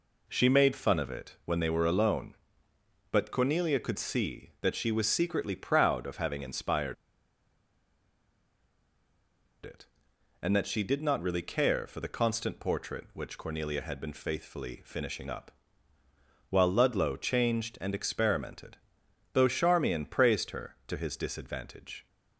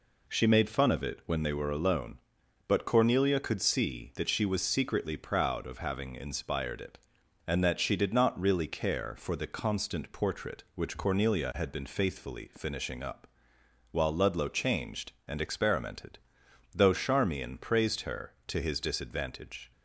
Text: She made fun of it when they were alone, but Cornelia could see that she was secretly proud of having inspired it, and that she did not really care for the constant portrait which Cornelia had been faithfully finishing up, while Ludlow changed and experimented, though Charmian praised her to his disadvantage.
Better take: second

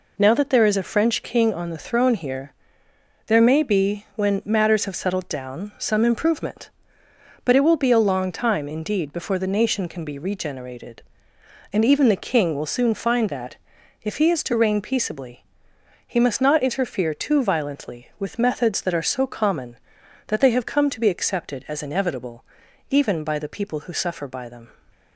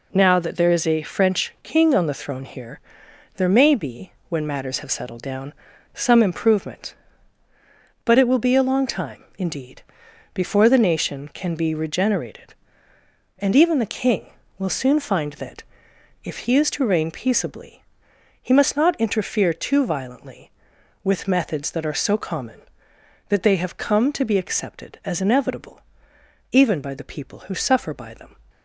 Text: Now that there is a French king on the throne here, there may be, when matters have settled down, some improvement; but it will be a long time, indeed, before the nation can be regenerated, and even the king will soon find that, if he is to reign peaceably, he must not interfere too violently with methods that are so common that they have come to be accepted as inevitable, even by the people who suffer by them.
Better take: neither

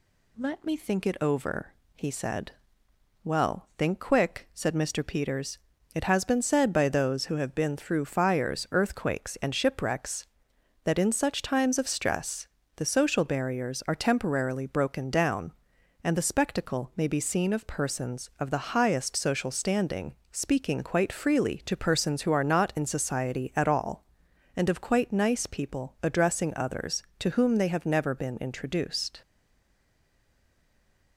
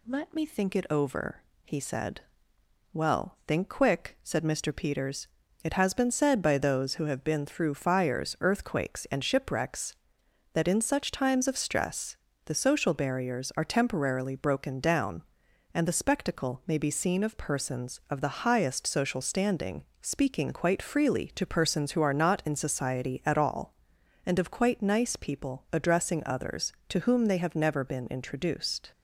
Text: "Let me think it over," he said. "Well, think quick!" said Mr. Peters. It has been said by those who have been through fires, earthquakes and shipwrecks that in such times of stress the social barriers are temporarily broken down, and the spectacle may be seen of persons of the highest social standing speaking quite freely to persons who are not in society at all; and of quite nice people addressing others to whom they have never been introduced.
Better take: second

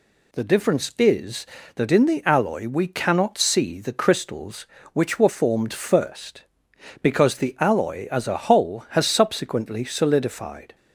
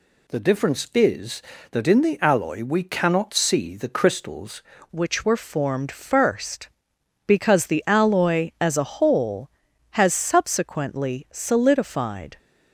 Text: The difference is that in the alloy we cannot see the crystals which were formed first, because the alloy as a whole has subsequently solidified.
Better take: first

